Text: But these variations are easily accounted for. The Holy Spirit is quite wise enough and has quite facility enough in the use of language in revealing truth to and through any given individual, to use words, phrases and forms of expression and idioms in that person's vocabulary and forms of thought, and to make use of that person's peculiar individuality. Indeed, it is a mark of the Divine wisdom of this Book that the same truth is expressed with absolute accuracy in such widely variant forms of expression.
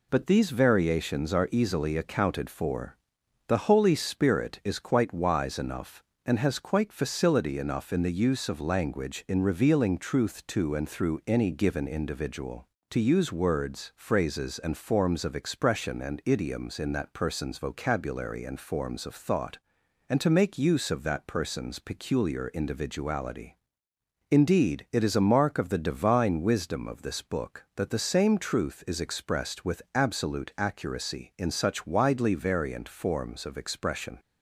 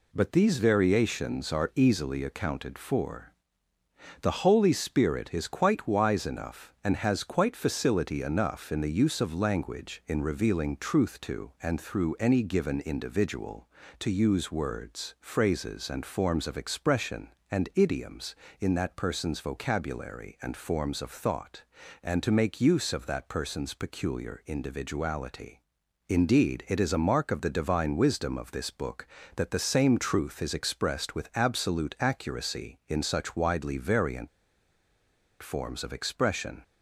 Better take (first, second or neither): first